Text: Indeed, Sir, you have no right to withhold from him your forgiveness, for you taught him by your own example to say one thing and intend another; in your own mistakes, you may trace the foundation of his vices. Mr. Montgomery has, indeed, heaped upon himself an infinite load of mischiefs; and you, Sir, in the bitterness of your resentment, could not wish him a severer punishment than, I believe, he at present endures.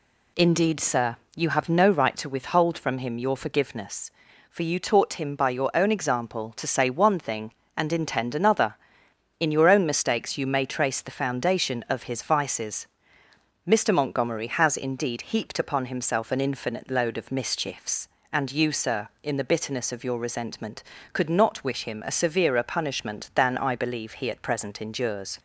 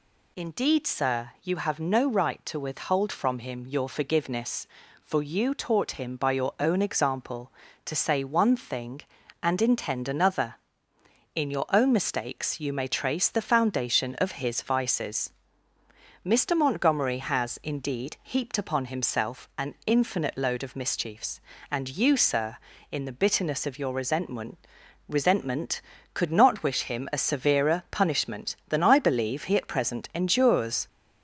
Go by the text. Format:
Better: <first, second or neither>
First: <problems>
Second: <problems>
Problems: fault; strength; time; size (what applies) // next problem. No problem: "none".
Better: first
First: none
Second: says "resentment" twice; at 25.0 s